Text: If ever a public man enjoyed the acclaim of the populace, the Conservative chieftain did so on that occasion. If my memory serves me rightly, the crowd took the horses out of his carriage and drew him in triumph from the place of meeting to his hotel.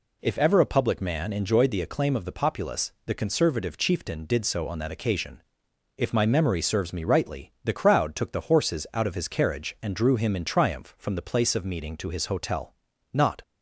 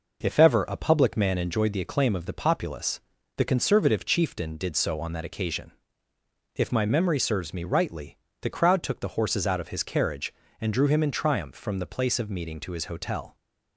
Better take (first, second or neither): second